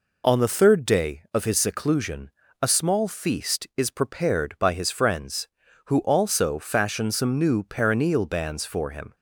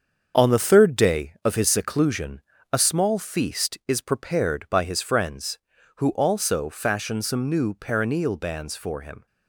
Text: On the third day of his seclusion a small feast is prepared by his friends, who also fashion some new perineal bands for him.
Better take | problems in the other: first | gets quieter; strong; throughout; 7.5 dB // pauses between "seclusion" and "a"; slight; at 2.4 s; 0.28 s long; slight in the first

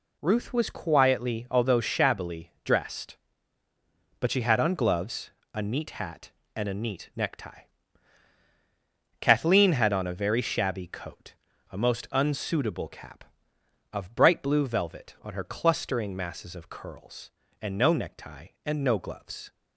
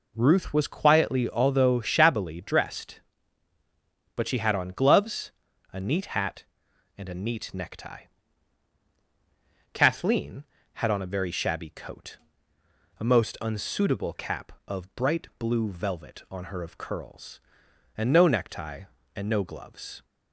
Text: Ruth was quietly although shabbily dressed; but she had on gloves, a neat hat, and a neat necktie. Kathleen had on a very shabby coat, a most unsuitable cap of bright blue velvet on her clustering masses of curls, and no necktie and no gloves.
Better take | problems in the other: first | skips "clustering masses"; at 16.6 s

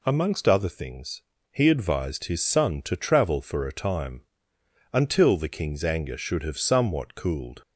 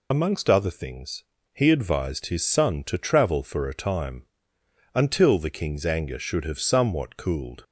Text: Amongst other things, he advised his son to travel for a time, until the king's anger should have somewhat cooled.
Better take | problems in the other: first | loses the start of "Amongst"; at 0.1 s; 55 ms

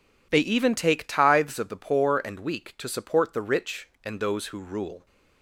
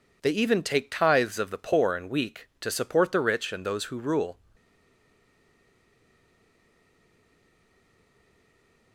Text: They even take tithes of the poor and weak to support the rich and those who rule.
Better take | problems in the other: first | stays silent after the last word; strong; from 4.5 s on; 4.4 s long

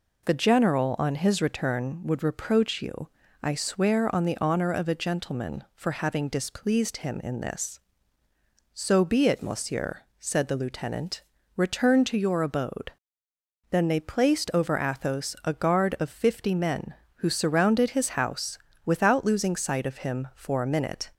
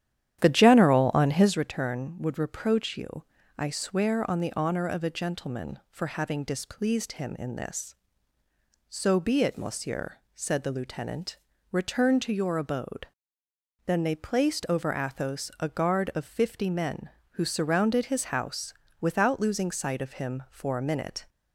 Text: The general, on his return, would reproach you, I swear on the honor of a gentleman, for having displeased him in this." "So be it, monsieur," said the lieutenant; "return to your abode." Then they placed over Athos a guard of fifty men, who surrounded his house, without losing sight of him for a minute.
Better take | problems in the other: first | starts louder than the rest; strong; until 1.5 s; 11 dB

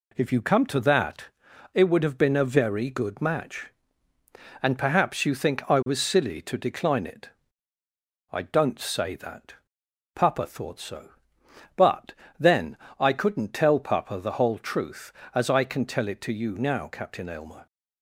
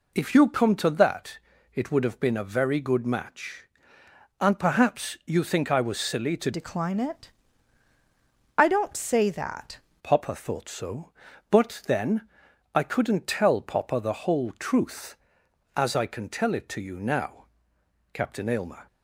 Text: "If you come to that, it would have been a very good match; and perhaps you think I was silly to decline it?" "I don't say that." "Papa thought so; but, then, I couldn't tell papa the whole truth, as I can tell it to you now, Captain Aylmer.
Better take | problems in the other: first | changes voice from "decline" to "that"; from 6.5 to 9.7 s; 3.2 s long

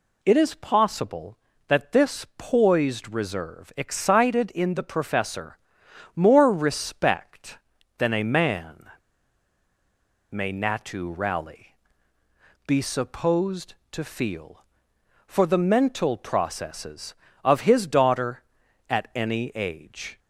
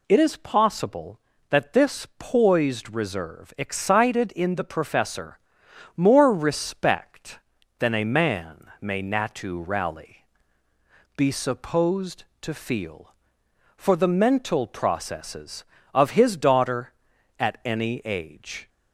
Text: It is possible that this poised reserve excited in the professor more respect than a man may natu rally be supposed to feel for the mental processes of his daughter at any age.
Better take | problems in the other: second | pauses between "professor" and "more"; noticeable; at 5.5 s; 0.58 s long; noticeable in the second // pauses between "man" and "may"; strong; at 8.8 s; 1.4 s long // pauses between "rally" and "be"; noticeable; at 11.7 s; 0.90 s long; noticeable in the second

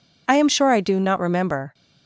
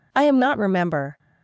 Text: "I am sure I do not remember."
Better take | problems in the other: first | skips "sure I do"; at 0.4 s

